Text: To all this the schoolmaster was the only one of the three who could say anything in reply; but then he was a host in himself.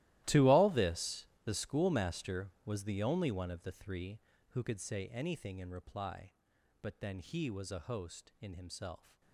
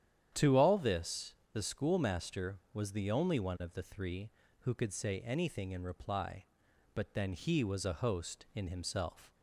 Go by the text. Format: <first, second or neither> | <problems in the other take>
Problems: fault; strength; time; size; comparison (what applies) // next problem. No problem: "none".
second | gets quieter; strong; throughout; 18.5 dB // starts louder than the rest; strong; until 1.4 s; 15.5 dB; strong in the second // pauses between "this" and "the"; slight; at 1.2 s; 0.18 s long; slight in the second